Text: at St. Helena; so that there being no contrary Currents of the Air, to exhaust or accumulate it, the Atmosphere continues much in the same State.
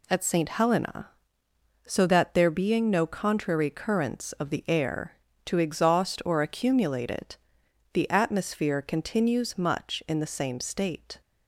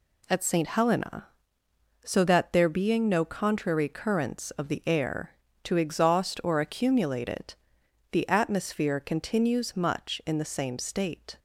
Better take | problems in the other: neither | none

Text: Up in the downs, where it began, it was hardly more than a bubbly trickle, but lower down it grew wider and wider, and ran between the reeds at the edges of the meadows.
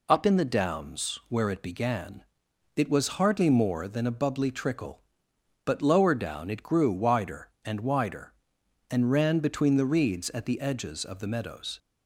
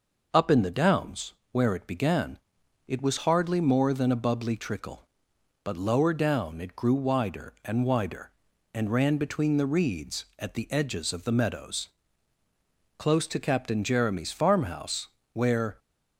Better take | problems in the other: first | goes on to say "Close to Captain Jeremy's farmhouse where"; strong; from 12.9 s on; 2.8 s long

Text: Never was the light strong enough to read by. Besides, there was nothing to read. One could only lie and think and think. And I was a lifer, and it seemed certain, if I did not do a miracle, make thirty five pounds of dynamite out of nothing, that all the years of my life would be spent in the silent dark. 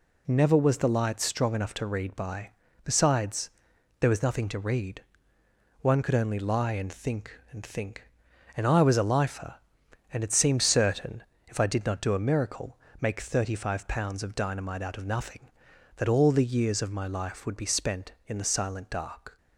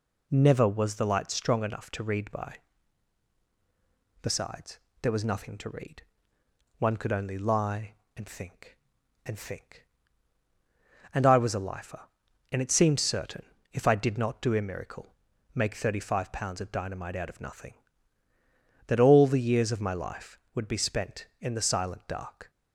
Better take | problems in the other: neither | none

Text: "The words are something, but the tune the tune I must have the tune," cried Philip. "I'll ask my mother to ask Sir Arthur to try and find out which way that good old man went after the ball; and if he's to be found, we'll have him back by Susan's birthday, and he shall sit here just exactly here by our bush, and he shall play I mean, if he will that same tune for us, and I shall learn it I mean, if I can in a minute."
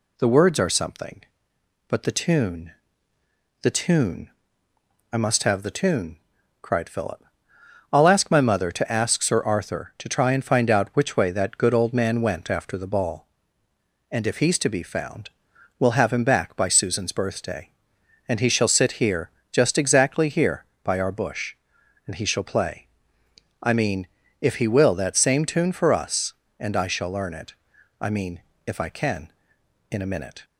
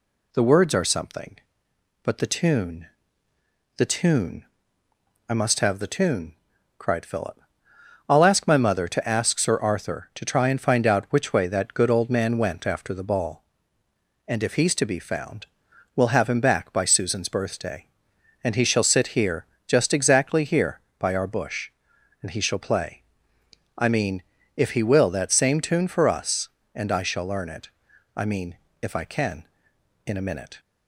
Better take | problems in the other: neither | pauses between "tune" and "the"; noticeable; the same in both // pauses between "tune" and "I"; noticeable; the same in both // pauses between "here" and "just"; slight; the same in both // pauses between "play" and "I"; noticeable; the same in both // pauses between "it" and "I"; noticeable; the same in both

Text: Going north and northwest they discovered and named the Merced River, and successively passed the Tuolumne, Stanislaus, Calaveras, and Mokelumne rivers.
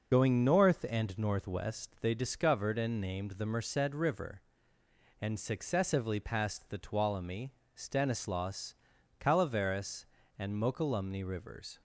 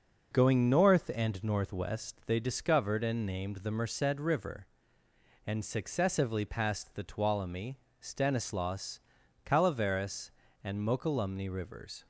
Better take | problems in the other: second | loses the start of "Going"; at 0.1 s; 60 ms

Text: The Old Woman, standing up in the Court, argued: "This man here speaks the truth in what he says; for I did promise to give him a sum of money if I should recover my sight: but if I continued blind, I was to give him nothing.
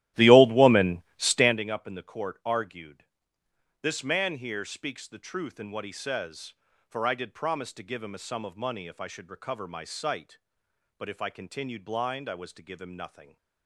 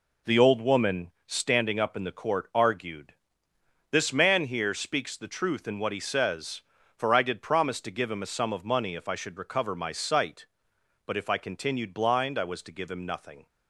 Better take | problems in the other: second | starts louder than the rest; strong; until 1.7 s; 14.5 dB

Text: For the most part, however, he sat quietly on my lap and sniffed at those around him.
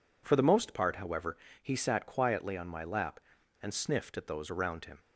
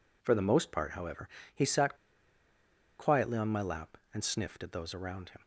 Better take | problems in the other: first | pauses between "sat" and "quietly"; at 1.9 s; 1.0 s long

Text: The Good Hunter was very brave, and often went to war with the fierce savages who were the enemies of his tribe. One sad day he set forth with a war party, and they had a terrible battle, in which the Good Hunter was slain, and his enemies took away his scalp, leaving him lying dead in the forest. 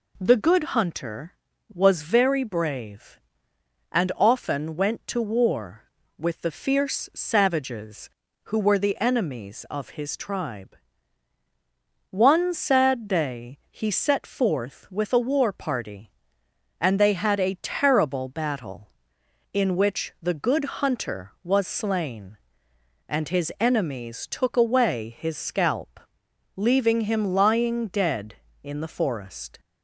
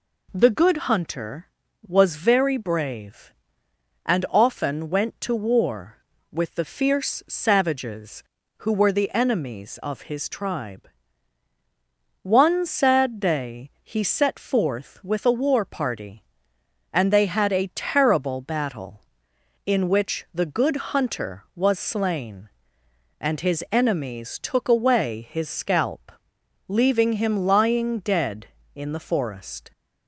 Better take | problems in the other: neither | pauses between "Good" and "Hunter"; slight; the same in both

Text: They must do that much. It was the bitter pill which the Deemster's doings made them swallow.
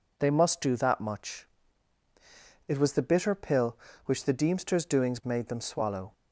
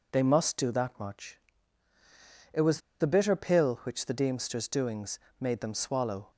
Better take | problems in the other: first | pauses between "was" and "the"; slight; at 2.7 s; 0.21 s long // pauses between "doings" and "made"; slight; at 5.1 s; 0.20 s long

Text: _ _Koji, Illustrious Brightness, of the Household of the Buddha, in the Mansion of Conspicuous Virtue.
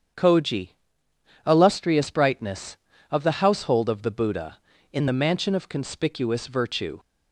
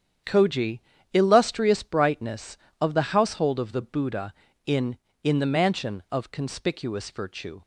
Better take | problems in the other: first | starts louder than the rest; strong; until 1.5 s; 8.5 dB; strong in the first // says "in" twice; at 5.2 s

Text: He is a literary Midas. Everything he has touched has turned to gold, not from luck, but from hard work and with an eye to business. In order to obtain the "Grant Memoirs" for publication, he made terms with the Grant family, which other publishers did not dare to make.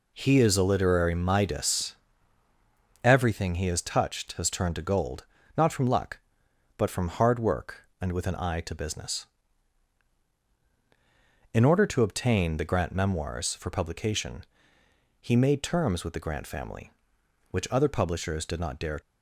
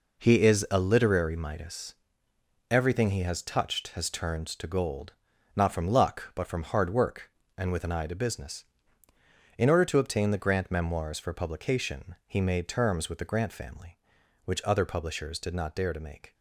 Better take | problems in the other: second | stops before "to make"; at 19.0 s

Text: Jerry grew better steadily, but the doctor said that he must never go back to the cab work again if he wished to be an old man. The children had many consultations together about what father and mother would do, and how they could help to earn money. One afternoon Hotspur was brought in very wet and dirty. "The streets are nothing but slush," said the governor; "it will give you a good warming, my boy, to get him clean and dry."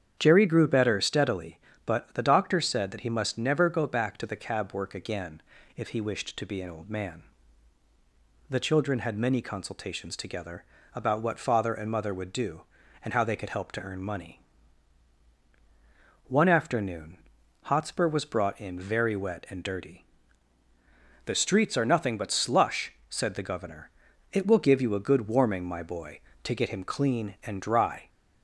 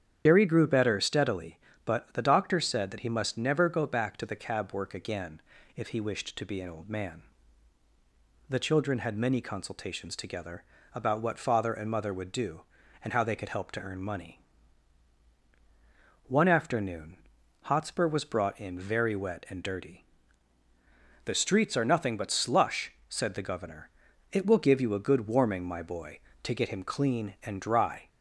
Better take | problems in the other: first | loses the start of "Jerry"; at 0.2 s; 75 ms // starts louder than the rest; strong; until 1.2 s; 8.5 dB; strong in the first // pauses between "again" and "if"; slight; at 5.3 s; 0.36 s long; slight in the first // pauses between "together" and "about"; slight; at 10.6 s; 0.30 s long; slight in the first // pauses between "afternoon" and "Hotspur"; noticeable; at 17.1 s; 0.46 s long; noticeable in the first

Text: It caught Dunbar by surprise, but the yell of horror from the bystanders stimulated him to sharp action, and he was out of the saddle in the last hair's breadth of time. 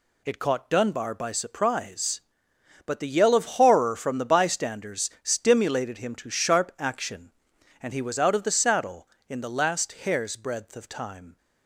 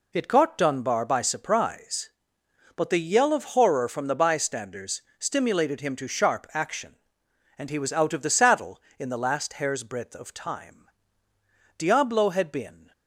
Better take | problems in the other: first | pauses between "bystanders" and "stimulated"; slight; at 4.9 s; 0.18 s long // goes on to say "Diablo had been"; noticeable; from 11.7 s on; 1.1 s long

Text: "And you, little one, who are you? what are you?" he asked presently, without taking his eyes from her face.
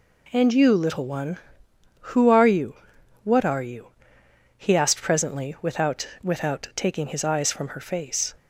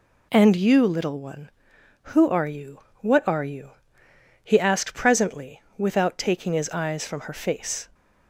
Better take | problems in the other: second | says "without" twice; at 6.2 s

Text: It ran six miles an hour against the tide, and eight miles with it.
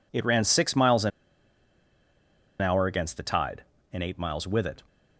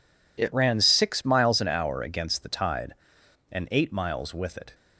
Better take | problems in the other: second | pauses between "an" and "hour"; strong; at 1.1 s; 1.5 s long

